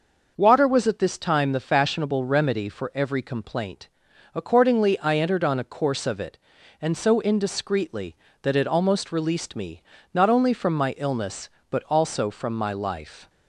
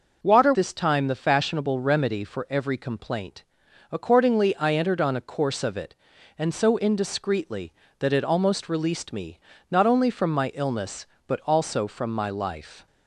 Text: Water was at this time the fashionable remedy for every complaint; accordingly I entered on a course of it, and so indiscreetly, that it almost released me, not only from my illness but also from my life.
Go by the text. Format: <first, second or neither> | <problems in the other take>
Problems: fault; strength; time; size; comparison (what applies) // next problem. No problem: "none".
first | skips "was at"; at 0.5 s